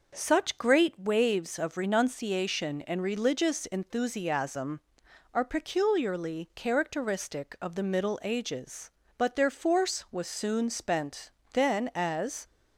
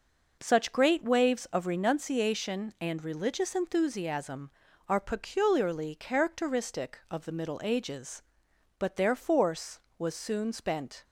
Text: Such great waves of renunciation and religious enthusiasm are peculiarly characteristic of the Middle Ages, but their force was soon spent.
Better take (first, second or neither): second